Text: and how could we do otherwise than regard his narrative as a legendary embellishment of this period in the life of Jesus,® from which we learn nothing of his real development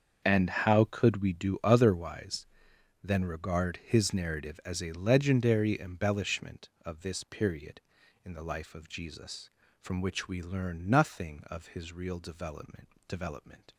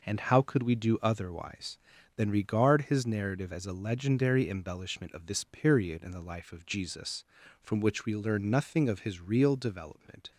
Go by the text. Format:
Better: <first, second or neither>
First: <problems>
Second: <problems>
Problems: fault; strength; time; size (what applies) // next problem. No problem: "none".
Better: second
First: starts louder than the rest; until 1.2 s; 7 dB // says "development" twice; at 13.0 s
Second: none